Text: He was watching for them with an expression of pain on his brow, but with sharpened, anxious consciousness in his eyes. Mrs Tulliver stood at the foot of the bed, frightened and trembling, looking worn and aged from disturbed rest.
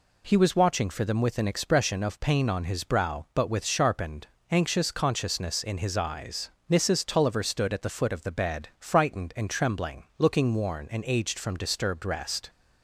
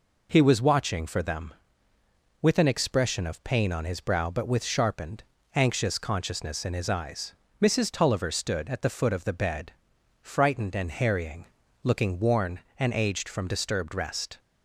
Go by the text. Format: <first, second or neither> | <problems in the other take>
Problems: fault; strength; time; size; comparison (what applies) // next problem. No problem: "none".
first | says "harrying" for "trembling"; at 10.8 s